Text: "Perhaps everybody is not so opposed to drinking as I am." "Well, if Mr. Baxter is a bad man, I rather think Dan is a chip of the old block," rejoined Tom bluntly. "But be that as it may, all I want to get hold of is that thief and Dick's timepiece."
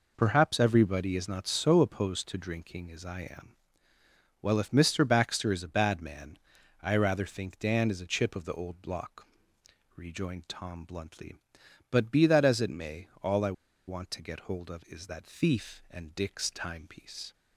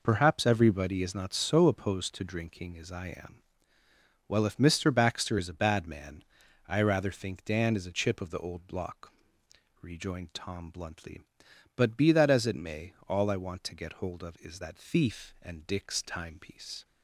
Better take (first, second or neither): second